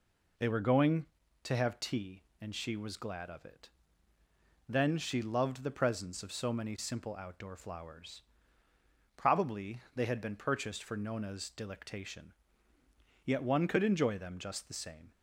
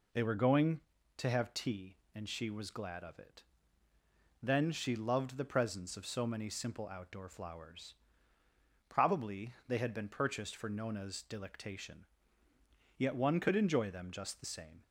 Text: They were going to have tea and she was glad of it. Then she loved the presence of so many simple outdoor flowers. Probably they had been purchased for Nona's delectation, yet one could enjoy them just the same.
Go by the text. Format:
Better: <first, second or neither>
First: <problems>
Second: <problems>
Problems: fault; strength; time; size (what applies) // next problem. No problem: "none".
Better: neither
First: pauses between "Probably" and "they"; slight; at 9.7 s; 0.16 s long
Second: pauses between "Probably" and "they"; slight; at 9.5 s; 0.16 s long